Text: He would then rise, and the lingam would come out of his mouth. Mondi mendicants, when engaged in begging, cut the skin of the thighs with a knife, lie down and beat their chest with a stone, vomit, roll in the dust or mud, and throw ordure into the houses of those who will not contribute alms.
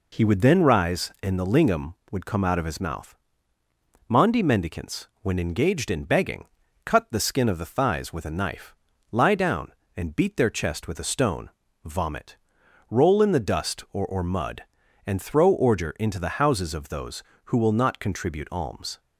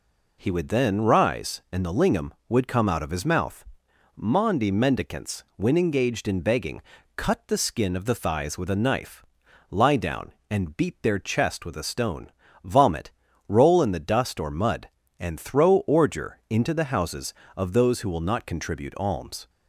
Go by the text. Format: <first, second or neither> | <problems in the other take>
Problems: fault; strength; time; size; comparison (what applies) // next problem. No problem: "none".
second | says "or" twice; at 14.0 s